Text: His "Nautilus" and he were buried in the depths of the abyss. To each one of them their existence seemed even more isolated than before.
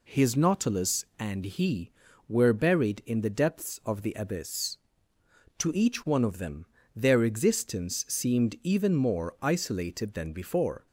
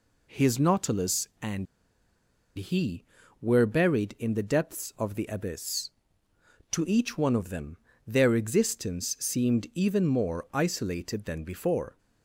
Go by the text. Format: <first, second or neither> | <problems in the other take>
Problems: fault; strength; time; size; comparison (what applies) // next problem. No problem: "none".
first | pauses between "and" and "he"; noticeable; at 1.6 s; 0.90 s long // pauses between "them" and "their"; slight; at 7.7 s; 0.32 s long; slight in the first